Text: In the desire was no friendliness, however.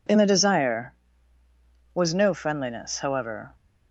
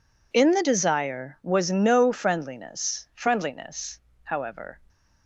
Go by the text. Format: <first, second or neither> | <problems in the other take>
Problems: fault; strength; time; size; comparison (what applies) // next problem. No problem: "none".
first | says "friendliness" twice; at 3.1 s